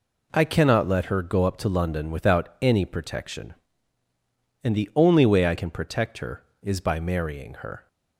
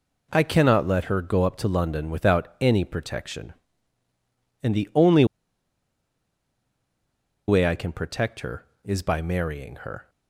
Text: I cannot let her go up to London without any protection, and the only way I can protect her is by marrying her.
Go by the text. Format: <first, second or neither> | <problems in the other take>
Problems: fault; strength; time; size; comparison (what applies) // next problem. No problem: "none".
first | pauses between "only" and "way"; strong; at 5.2 s; 2.2 s long